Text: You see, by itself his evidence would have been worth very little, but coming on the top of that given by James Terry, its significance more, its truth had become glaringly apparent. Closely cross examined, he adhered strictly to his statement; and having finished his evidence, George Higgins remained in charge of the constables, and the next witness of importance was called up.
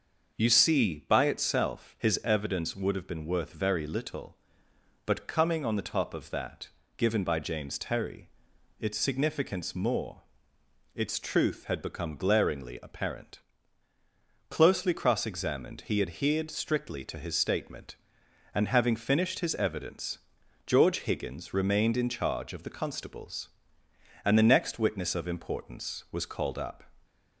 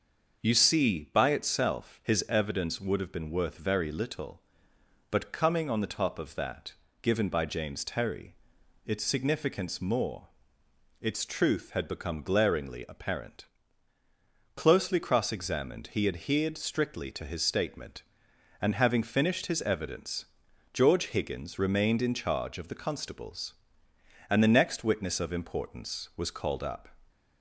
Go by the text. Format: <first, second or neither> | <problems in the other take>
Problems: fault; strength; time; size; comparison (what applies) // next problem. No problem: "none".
neither | starts louder than the rest; the same in both // pauses between "that" and "given"; slight; the same in both